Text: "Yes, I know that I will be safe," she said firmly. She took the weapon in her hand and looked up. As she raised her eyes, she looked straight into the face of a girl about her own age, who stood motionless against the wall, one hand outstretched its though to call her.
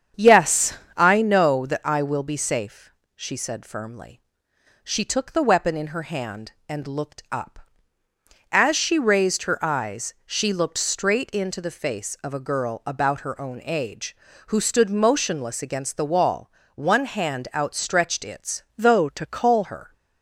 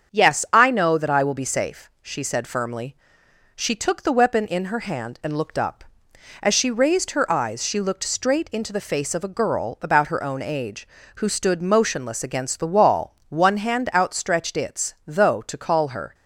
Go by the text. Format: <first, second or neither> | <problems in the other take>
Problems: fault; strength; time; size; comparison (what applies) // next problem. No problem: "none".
second | starts louder than the rest; strong; until 1.3 s; 8 dB; strong in the second // changes voice from "though" to "call"; from 18.7 to 19.6 s; 0.9 s long